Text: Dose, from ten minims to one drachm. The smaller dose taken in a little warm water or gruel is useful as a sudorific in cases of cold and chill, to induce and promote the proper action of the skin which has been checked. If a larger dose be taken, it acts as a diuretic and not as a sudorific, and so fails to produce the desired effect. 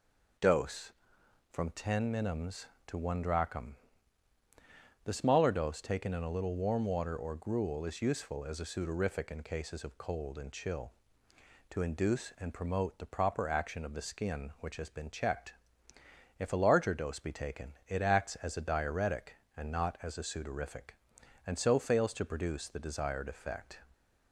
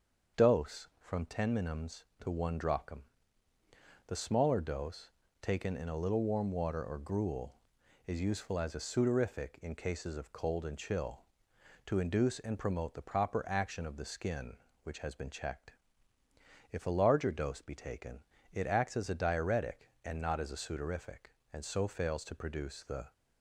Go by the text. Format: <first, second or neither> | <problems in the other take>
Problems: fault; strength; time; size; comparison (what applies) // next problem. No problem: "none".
first | starts louder than the rest; until 1.4 s; 7 dB // pauses between "dose" and "taken"; slight; at 5.1 s; 0.32 s long // stops before "desired effect"; at 23.1 s